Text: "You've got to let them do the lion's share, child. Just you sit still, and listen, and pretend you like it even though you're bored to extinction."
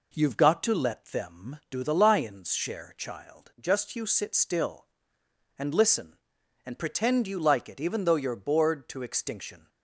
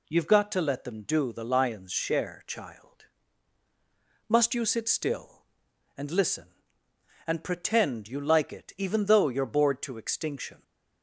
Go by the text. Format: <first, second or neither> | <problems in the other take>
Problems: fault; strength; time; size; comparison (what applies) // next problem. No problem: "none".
first | says "Must" for "Just"; at 4.2 s